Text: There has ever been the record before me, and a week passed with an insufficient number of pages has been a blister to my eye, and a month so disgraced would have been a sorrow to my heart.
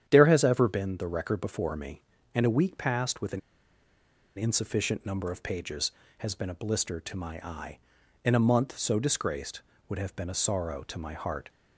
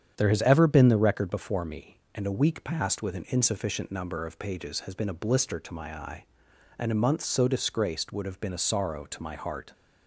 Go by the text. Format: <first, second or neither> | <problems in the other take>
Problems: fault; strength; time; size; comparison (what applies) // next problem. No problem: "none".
second | starts louder than the rest; strong; until 1.0 s; 9.5 dB; strong in the second // pauses between "an" and "insufficient"; at 3.4 s; 0.98 s long